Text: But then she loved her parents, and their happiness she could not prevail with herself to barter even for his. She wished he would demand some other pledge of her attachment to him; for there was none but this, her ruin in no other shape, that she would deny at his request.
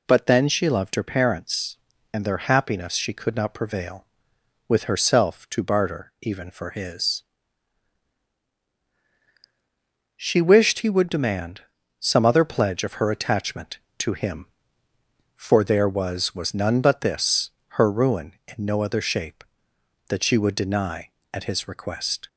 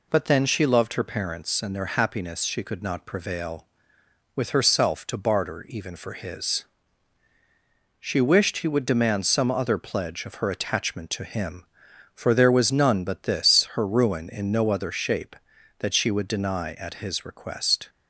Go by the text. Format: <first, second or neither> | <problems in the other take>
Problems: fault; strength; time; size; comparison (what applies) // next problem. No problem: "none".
second | pauses between "demand" and "some"; at 11.6 s; 0.38 s long // says "was" twice; at 16.3 s